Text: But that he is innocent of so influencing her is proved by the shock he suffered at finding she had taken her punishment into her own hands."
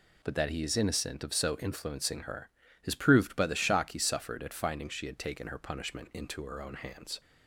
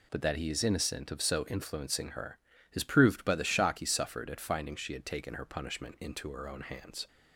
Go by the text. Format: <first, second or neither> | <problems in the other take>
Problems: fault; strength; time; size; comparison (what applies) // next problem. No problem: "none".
neither | none